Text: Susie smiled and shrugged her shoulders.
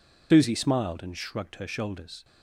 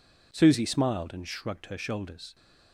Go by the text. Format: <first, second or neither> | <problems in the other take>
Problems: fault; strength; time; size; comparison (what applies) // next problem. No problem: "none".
second | loses the start of "Susie"; at 0.3 s; 80 ms